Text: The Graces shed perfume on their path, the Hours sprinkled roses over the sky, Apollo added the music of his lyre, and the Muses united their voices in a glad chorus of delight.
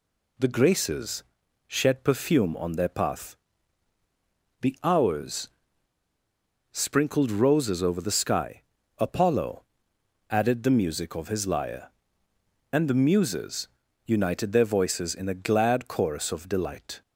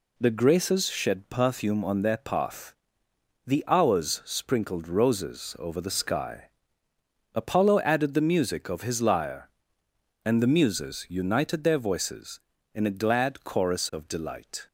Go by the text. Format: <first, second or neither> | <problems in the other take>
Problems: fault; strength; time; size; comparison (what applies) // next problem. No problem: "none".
second | pauses between "Graces" and "shed"; at 1.2 s; 0.44 s long // pauses between "Hours" and "sprinkled"; at 5.4 s; 1.2 s long // pauses between "Apollo" and "added"; noticeable; at 9.6 s; 0.66 s long // pauses between "Muses" and "united"; at 13.6 s; 0.38 s long